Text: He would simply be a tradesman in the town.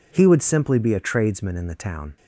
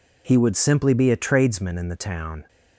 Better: neither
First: none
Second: none

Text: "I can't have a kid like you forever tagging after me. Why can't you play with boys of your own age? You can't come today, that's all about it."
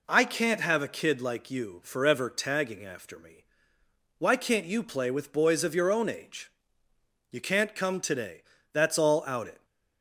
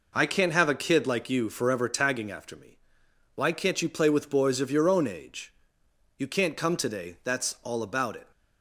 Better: second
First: says "out" for "about"; at 9.2 s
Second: none

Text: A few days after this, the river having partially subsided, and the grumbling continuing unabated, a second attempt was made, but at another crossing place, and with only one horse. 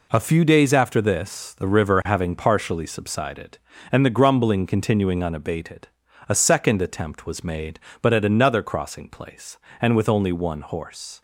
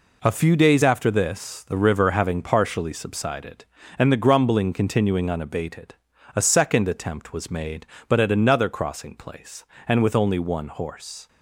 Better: neither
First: none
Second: none

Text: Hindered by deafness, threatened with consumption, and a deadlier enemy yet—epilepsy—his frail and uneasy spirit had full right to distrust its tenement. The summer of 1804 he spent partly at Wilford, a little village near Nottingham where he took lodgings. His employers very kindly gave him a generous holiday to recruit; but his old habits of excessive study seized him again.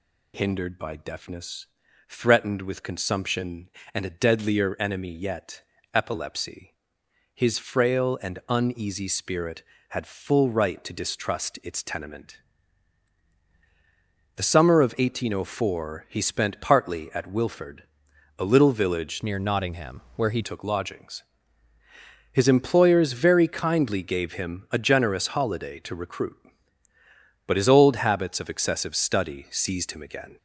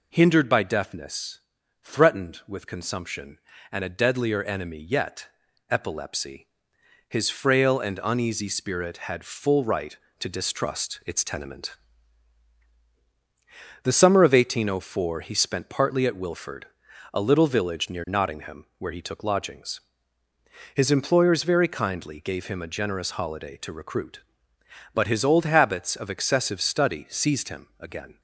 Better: second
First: changes voice from "near" to "he"; from 19.2 to 20.4 s; 1.2 s long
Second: none

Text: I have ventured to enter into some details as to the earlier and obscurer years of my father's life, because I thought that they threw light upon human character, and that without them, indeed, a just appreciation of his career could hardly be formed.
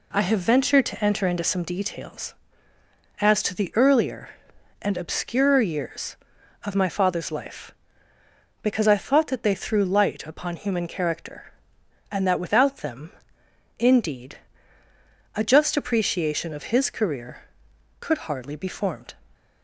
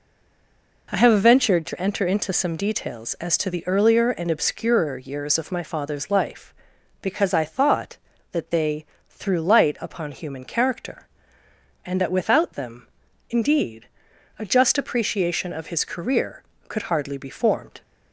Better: first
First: none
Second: stays silent before the first word; slight; until 0.8 s; 0.8 s long // pauses between "they" and "threw"; slight; at 8.8 s; 0.20 s long

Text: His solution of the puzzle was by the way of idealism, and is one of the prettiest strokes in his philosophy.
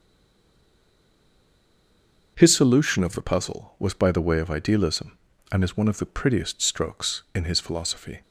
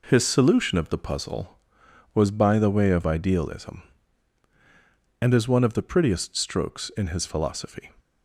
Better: second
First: stays silent before the first word; until 2.3 s; 2.3 s long // starts louder than the rest; until 3.3 s; 6 dB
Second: none

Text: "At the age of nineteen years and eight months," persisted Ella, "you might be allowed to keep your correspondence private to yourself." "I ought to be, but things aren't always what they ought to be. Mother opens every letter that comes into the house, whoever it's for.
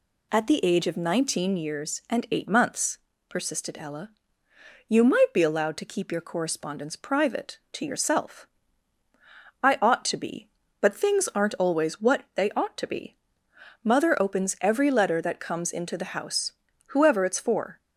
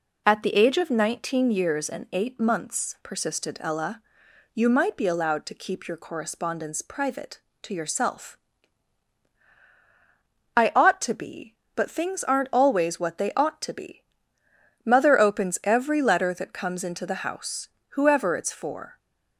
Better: neither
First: none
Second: none

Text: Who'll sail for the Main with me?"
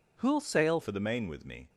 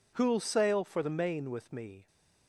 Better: second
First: changes voice at "for"; from 0.8 s on; 0.8 s long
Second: none

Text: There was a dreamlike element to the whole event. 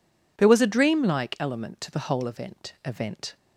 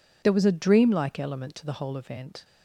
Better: second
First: says "event" twice; at 2.8 s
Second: none

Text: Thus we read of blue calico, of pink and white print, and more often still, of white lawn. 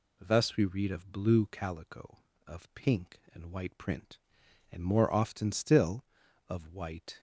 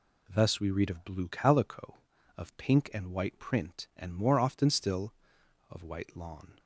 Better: second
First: stops before "lawn"; at 7.1 s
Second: none

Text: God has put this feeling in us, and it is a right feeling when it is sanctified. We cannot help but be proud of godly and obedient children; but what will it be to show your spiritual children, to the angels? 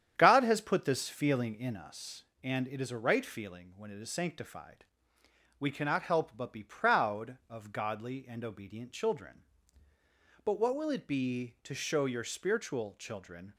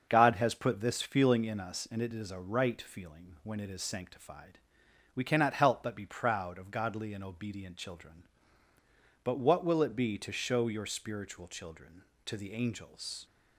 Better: second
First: starts louder than the rest; strong; until 1.1 s; 9 dB // stops before "to the angels"; at 13.5 s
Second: starts louder than the rest; until 1.1 s; 6.5 dB

